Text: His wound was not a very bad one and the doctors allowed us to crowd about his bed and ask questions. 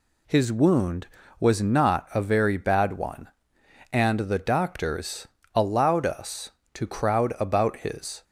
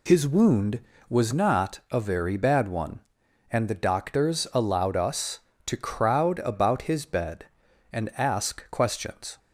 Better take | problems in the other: second | pauses between "doctors" and "allowed"; slight; at 5.2 s; 0.26 s long // stops before "bed and ask questions"; at 8.2 s

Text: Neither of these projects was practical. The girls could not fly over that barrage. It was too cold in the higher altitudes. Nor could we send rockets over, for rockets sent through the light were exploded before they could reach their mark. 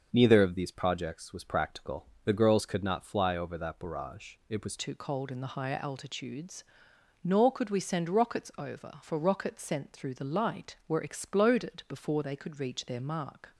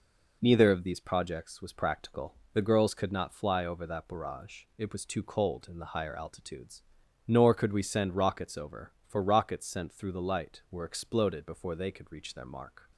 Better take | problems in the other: second | starts louder than the rest; until 1.1 s; 6.5 dB // changes voice at "too"; from 4.7 s on; 8.8 s long

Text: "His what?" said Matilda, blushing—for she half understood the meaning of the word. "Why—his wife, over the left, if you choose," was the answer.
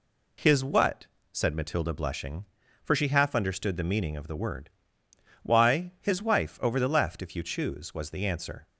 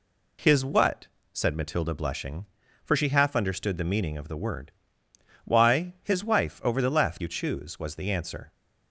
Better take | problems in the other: first | skips "if"; at 7.2 s

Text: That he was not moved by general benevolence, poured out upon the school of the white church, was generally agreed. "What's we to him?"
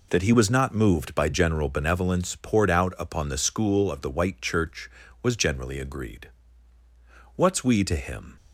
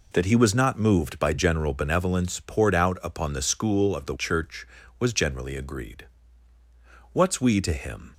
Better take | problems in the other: first | skips "white"; at 4.1 s

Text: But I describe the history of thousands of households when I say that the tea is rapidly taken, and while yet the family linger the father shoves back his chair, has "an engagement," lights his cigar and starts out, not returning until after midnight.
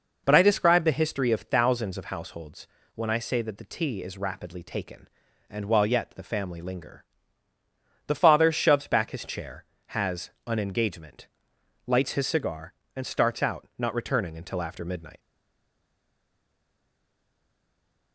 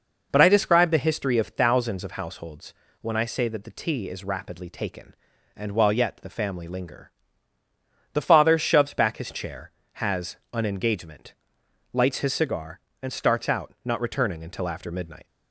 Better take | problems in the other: second | pauses between "households" and "when"; slight; at 2.6 s; 0.28 s long; slight in the second // pauses between "linger" and "the"; at 7.0 s; 1.0 s long; also in the second // pauses between "has" and "an"; slight; at 10.2 s; 0.18 s long; slight in the second // stays silent after the last word; strong; from 15.1 s on; 3.0 s long

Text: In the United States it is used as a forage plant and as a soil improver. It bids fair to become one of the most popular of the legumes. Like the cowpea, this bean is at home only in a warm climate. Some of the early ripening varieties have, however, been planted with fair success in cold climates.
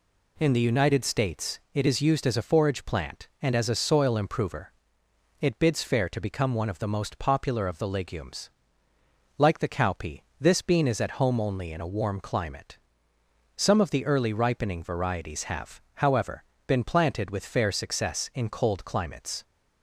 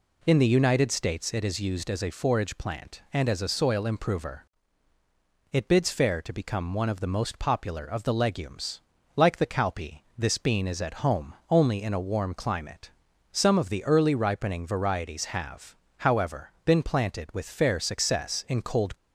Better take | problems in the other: first | pauses between "home" and "only"; slight; at 11.3 s; 0.16 s long // stops before "climates"; at 18.9 s

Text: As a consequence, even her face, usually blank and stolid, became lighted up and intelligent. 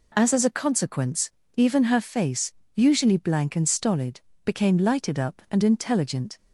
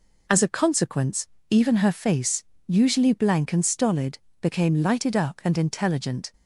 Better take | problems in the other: second | says "As" twice; at 0.3 s

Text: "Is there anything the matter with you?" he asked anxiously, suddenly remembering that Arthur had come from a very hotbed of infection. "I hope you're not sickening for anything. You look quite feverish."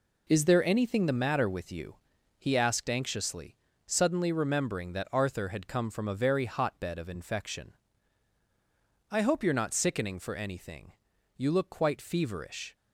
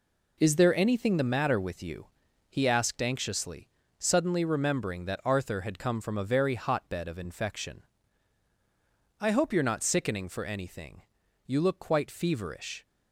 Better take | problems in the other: neither | none

